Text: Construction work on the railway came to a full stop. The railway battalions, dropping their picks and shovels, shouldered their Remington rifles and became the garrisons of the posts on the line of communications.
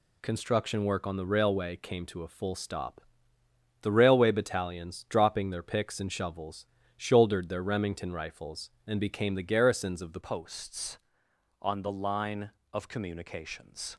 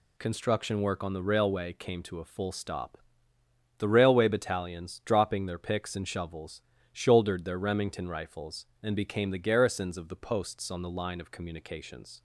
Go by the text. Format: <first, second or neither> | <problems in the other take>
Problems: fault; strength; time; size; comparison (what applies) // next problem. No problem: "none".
second | changes voice at "posts"; from 10.2 s on; 3.7 s long